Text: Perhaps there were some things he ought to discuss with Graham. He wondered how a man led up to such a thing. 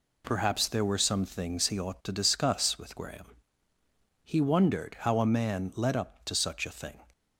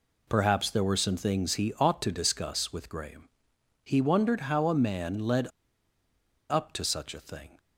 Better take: first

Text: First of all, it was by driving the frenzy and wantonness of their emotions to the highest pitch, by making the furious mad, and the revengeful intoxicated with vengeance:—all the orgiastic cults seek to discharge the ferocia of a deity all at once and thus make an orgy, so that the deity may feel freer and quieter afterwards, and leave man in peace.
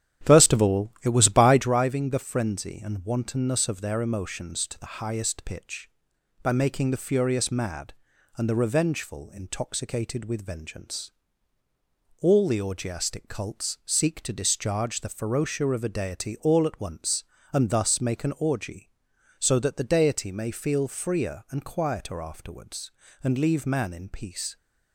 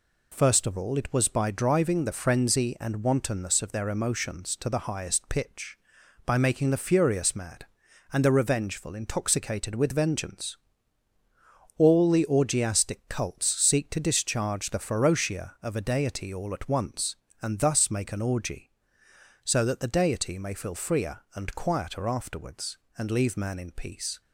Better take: second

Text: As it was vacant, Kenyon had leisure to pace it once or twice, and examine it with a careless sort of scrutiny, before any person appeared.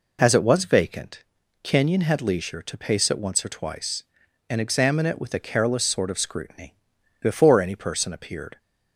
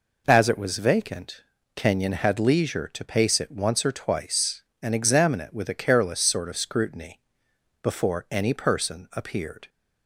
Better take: neither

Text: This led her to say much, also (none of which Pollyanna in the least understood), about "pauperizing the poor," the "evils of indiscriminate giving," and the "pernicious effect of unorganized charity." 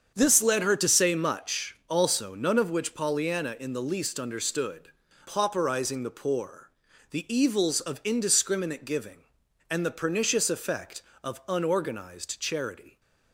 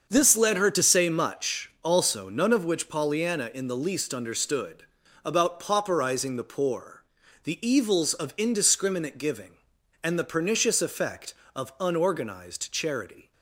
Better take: second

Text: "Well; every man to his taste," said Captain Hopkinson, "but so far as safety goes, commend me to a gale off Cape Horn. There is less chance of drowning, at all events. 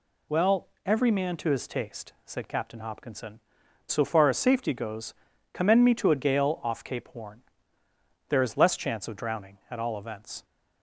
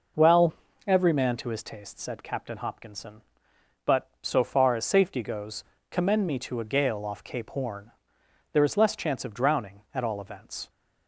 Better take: second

